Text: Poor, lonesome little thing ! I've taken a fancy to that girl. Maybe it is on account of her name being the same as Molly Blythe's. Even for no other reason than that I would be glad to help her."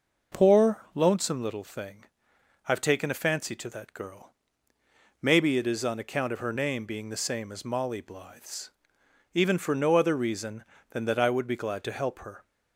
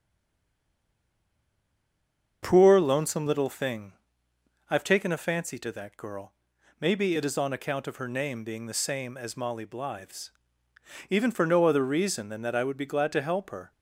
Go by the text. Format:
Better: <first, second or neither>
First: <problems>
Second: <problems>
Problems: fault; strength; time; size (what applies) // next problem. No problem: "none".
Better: first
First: none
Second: stays silent before the first word; until 2.4 s; 2.4 s long // starts louder than the rest; until 3.4 s; 7 dB